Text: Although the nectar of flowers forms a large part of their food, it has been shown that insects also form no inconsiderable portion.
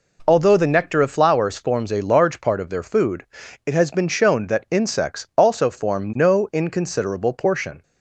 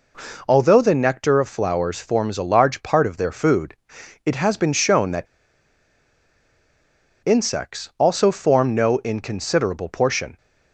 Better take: first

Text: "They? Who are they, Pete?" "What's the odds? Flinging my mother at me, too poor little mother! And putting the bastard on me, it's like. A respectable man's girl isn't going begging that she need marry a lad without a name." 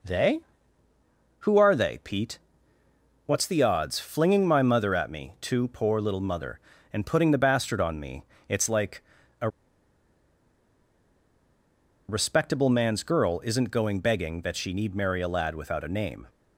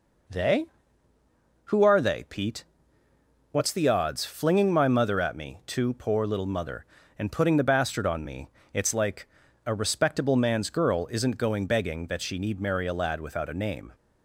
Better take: second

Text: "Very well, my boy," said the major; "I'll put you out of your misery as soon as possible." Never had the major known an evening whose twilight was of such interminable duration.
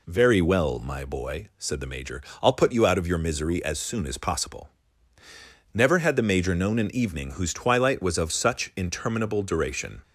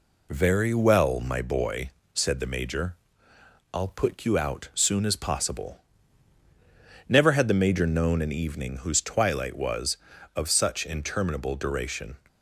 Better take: first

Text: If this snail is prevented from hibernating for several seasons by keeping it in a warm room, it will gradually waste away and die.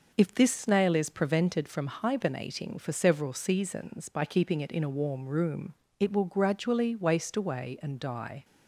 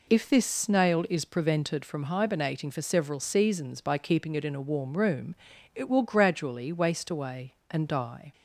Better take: neither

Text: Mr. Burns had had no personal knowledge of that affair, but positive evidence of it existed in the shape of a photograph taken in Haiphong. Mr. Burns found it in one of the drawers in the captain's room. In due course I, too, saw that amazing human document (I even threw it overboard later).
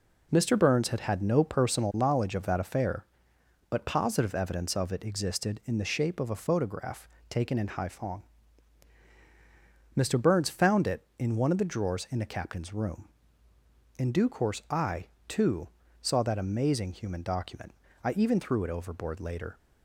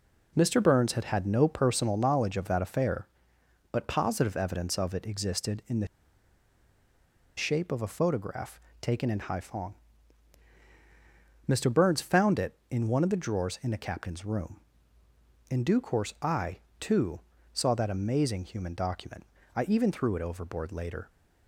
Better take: first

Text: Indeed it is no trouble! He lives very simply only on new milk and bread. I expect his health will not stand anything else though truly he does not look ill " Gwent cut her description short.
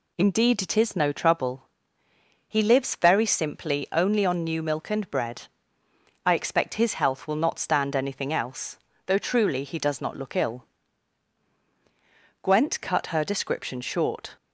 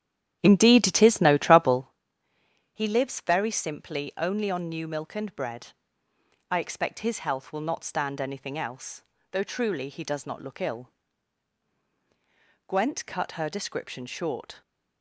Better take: first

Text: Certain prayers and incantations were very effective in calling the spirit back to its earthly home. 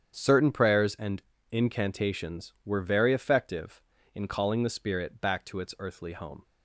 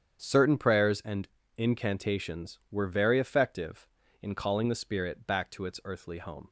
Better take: neither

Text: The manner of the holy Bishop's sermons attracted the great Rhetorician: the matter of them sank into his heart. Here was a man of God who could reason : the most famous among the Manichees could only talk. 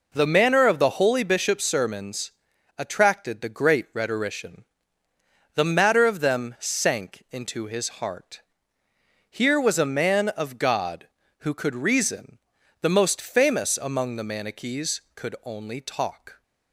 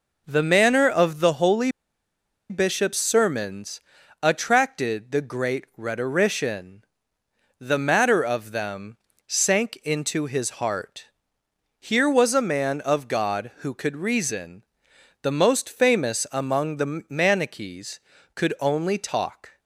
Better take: first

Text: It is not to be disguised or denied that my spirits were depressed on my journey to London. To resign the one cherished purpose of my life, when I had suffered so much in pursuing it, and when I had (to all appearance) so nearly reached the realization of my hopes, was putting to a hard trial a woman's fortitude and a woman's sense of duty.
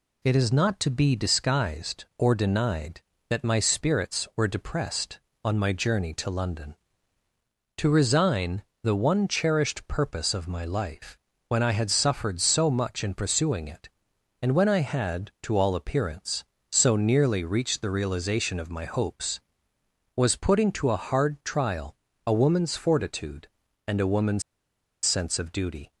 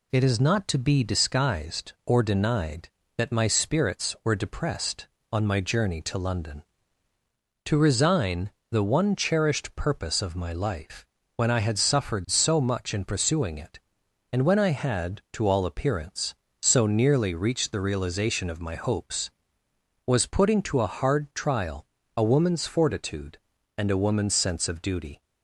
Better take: second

